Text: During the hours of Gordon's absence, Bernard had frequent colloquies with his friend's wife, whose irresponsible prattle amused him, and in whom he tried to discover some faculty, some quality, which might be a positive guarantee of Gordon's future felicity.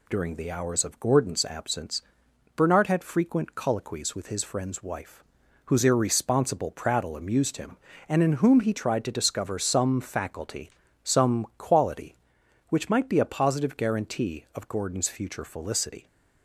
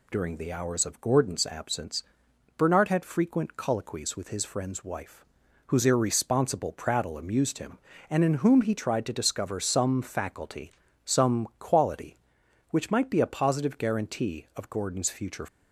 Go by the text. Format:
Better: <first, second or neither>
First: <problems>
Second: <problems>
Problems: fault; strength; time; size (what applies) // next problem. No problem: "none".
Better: first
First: none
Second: stops before "felicity"; at 15.4 s